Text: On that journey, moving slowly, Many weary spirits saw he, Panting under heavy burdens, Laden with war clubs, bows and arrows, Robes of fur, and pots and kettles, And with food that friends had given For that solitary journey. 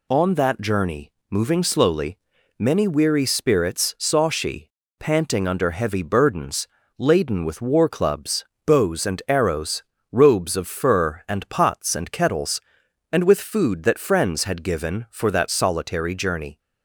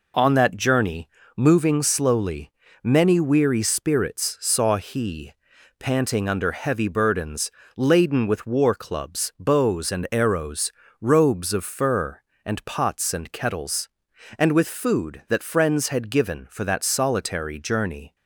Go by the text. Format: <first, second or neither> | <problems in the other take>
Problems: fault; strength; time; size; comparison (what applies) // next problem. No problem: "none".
second | says "she" for "he"; at 4.2 s